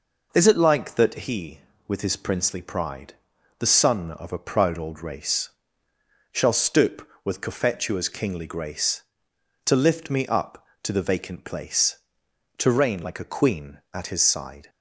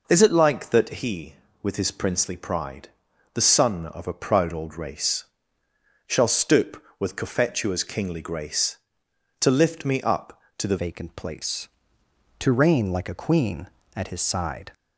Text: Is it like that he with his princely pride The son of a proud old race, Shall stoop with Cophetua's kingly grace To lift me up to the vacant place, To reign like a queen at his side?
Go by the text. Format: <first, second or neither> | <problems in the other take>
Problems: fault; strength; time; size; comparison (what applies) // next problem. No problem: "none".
first | pauses between "pride" and "The"; at 2.8 s; 0.44 s long; also in the first // changes voice at "vacant"; from 10.7 s on; 4.0 s long